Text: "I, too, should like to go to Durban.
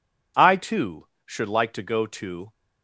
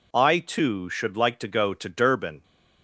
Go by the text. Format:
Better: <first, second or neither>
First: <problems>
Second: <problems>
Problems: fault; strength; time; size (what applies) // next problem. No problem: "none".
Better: second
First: stops before "Durban"; at 2.5 s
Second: none